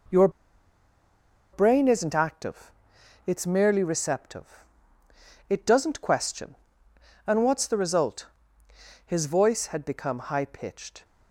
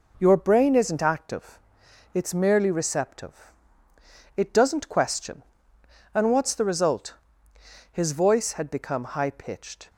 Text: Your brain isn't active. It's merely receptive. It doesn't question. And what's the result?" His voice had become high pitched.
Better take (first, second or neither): second